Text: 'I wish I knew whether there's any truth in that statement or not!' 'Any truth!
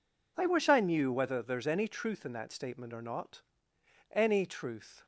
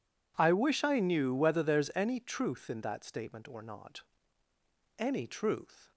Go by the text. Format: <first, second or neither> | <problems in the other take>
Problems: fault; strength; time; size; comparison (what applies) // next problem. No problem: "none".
neither | none